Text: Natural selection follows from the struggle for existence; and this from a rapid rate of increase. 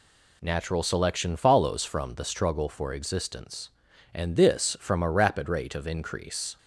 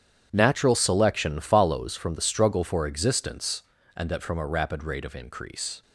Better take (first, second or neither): first